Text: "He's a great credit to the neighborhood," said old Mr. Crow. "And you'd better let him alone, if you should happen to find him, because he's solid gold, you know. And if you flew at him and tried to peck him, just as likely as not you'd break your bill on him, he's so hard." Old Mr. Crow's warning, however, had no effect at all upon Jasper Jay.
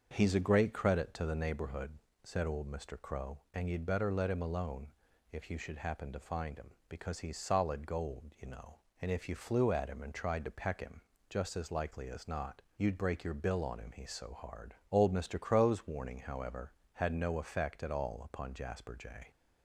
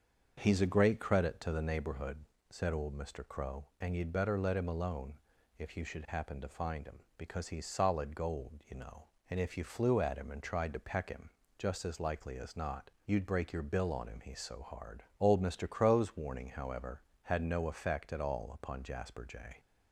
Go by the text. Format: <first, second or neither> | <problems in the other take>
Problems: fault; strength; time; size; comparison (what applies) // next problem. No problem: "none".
neither | starts louder than the rest; the same in both // pauses between "not" and "you'd"; slight; the same in both